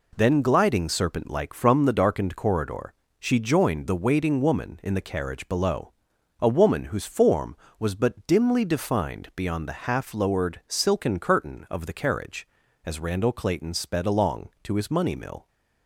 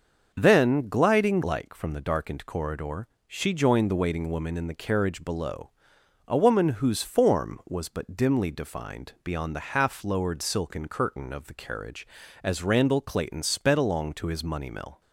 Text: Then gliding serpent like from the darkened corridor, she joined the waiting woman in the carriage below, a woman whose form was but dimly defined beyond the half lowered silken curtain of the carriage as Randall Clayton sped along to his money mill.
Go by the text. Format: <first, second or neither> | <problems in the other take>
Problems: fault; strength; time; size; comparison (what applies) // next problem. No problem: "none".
first | starts louder than the rest; until 1.3 s; 6.5 dB // skips "serpent"; at 1.4 s